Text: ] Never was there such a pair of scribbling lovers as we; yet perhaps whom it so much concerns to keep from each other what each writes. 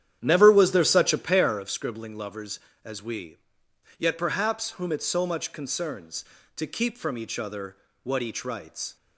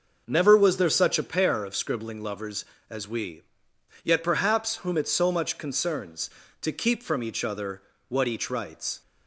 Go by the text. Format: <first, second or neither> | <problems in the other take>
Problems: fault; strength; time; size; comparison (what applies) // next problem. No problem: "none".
second | starts louder than the rest; strong; until 1.8 s; 10 dB // pauses between "other" and "what"; slight; at 7.7 s; 0.26 s long; slight in the second